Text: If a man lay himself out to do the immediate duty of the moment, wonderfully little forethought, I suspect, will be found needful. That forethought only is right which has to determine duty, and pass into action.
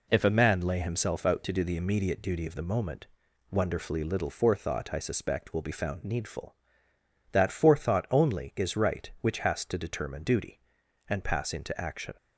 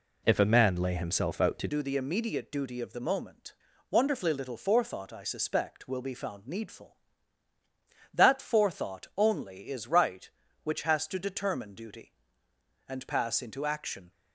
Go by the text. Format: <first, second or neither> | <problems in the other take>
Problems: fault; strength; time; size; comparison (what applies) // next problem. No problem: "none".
first | changes voice at "do"; from 1.6 s on; 12.5 s long